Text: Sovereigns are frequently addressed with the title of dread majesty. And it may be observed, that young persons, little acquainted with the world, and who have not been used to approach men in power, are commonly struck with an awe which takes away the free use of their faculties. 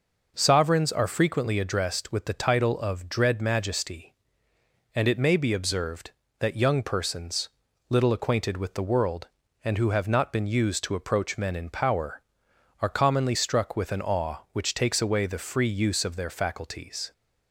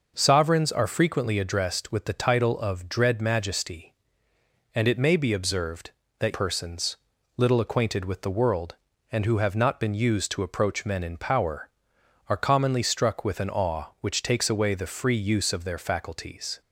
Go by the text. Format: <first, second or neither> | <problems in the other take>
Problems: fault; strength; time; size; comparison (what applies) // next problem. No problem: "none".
first | skips "young"; at 6.3 s